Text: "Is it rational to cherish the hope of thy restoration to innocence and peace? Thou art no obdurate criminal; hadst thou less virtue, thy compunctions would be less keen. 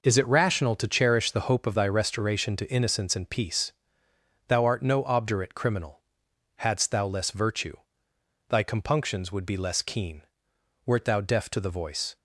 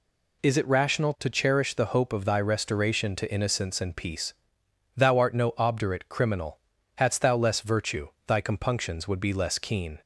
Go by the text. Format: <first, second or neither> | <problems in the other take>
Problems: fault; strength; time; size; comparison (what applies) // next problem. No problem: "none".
second | goes on to say "Wert thou deaf to the voice"; from 10.8 s on; 1.3 s long